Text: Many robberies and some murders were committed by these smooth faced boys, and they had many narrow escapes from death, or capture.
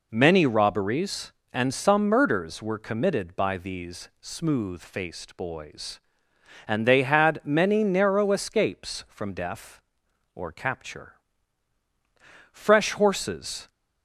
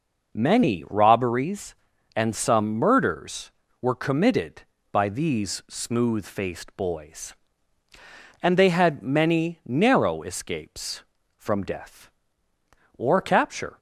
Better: second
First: goes on to say "Fresh horses"; noticeable; from 12.5 s on; 1.1 s long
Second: none

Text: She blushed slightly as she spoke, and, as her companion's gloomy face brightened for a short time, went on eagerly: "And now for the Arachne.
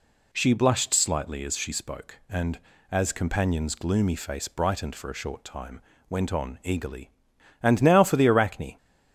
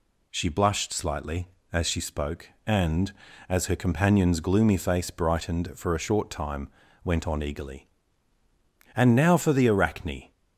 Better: second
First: skips "her"; at 3.1 s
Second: none

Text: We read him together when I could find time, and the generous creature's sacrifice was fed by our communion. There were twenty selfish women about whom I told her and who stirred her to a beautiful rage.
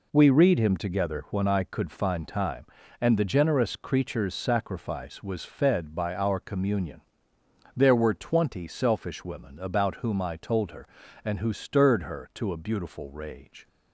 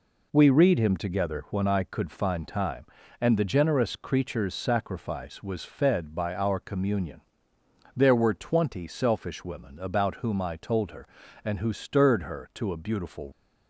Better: first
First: none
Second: stops before "rage"; at 13.3 s

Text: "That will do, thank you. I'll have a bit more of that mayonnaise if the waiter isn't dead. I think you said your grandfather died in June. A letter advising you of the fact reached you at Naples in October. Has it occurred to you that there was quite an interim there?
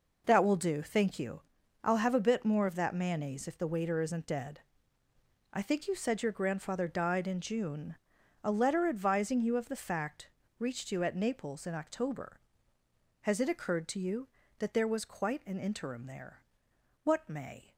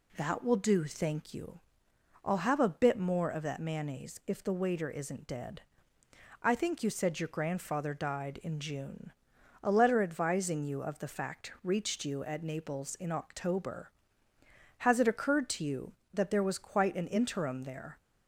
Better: second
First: pauses between "fact" and "reached"; slight; at 10.2 s; 0.30 s long // goes on to say "What may"; noticeable; from 17.0 s on; 0.70 s long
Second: none

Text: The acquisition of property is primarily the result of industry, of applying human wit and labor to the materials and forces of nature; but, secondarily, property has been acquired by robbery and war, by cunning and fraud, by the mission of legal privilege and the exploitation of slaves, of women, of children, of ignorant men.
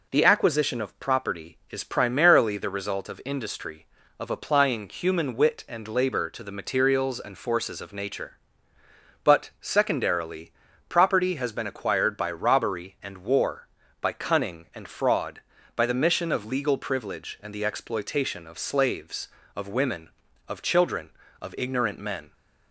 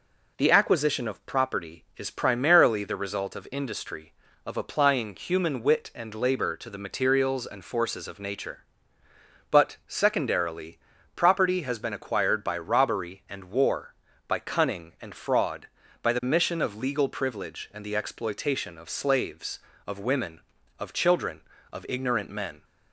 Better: neither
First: none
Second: none

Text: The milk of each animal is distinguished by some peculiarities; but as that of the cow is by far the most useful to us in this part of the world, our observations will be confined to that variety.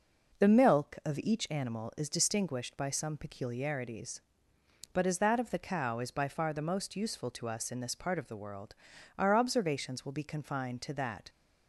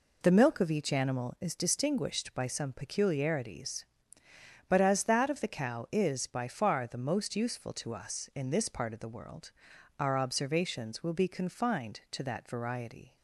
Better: second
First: stops before "variety"; at 11.2 s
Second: none

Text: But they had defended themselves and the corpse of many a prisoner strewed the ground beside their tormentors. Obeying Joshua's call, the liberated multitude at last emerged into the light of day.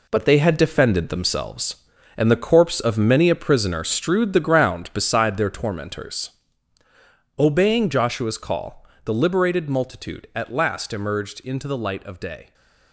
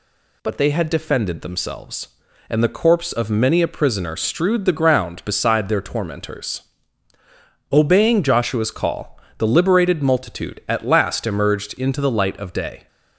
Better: second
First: gets quieter; strong; throughout; 9.5 dB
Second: none

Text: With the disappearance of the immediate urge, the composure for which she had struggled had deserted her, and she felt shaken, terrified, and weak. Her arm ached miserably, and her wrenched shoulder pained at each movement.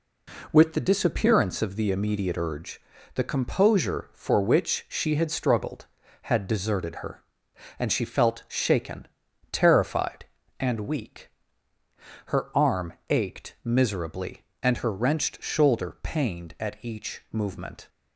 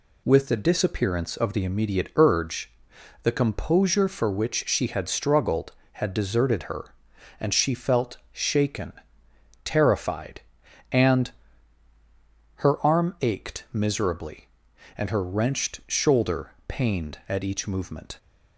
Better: first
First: none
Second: skips "weak"; at 11.9 s // pauses between "shoulder" and "pained"; slight; at 16.5 s; 0.16 s long

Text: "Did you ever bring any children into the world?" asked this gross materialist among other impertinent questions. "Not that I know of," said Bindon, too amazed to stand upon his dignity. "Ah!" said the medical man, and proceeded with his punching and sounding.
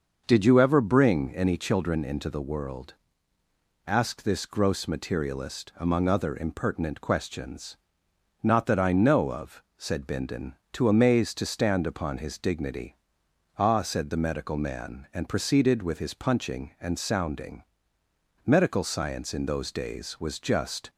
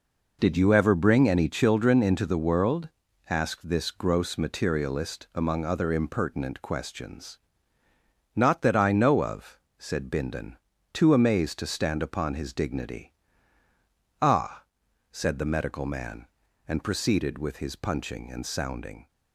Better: second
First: starts louder than the rest; until 1.2 s; 6 dB // goes on to say "Medical science in those days was just"; strong; from 18.4 s on; 2.4 s long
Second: none

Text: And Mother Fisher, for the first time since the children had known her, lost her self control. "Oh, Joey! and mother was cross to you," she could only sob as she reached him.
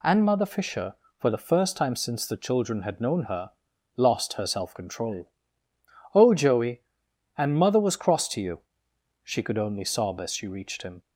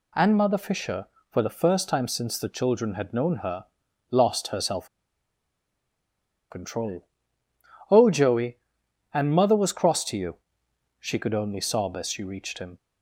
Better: first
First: none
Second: pauses between "self" and "control"; strong; at 4.8 s; 1.6 s long

